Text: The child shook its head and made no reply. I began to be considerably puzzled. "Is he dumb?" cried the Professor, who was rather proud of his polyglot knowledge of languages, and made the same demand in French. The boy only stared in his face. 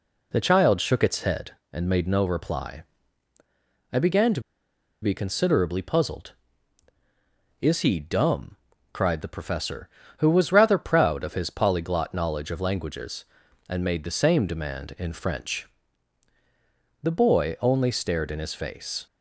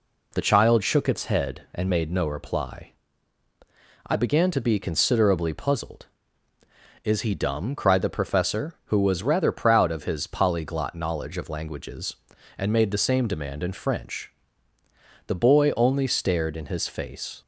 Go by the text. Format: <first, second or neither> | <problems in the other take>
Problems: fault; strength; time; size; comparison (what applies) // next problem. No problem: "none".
second | pauses between "to" and "be"; noticeable; at 4.3 s; 0.62 s long